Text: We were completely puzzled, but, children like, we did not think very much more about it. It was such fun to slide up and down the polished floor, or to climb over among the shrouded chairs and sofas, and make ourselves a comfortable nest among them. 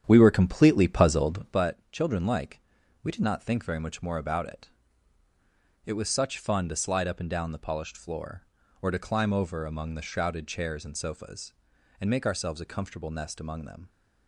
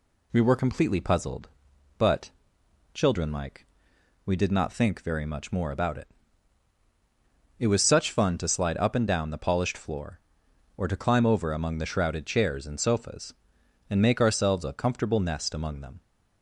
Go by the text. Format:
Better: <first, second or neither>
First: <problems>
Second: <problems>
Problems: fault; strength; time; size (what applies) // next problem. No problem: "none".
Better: second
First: starts louder than the rest; strong; until 1.6 s; 9.5 dB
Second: none